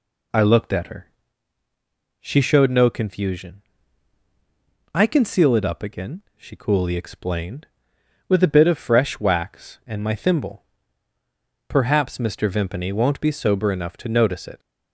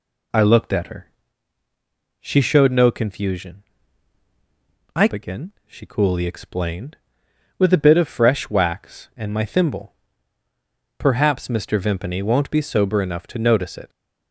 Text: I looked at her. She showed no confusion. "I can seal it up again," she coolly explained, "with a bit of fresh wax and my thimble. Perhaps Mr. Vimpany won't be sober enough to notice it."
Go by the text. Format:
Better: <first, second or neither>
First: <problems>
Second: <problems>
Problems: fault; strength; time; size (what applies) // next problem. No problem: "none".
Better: first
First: none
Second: skips "can seal it up"; at 5.0 s